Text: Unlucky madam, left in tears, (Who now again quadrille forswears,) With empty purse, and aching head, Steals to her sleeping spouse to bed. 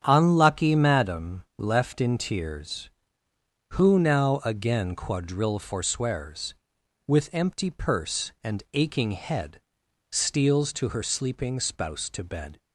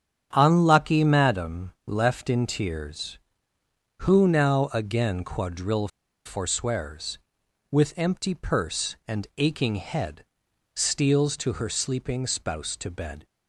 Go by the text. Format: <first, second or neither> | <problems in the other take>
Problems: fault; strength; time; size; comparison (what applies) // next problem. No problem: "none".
first | starts louder than the rest; strong; until 1.3 s; 8.5 dB; strong in the first // pauses between "quadrille" and "forswears"; slight; at 5.8 s; 0.36 s long